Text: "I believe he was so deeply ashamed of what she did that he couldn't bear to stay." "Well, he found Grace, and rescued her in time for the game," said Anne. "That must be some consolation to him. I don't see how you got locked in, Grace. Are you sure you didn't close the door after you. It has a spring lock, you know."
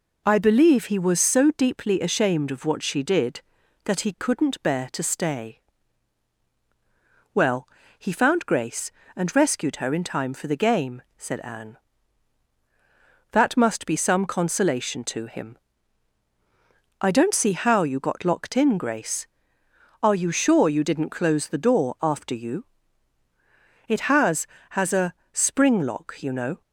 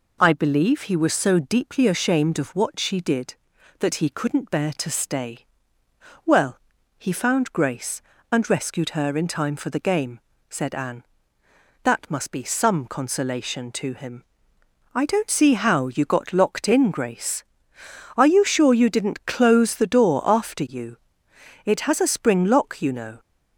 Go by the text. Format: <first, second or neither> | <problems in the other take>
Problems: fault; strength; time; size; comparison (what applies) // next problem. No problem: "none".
second | says "has" twice; at 24.6 s // pauses between "a" and "spring"; slight; at 25.1 s; 0.20 s long